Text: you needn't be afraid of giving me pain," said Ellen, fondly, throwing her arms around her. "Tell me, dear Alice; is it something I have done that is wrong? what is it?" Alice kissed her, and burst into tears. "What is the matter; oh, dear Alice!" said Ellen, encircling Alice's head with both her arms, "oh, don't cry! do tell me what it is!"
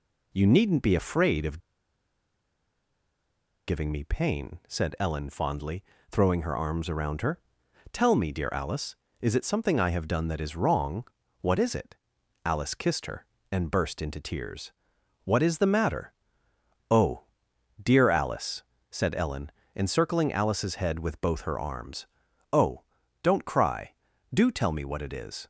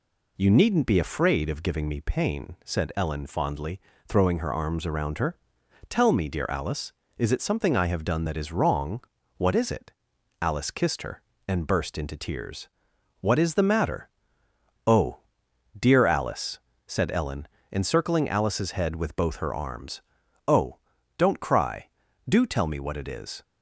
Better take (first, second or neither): second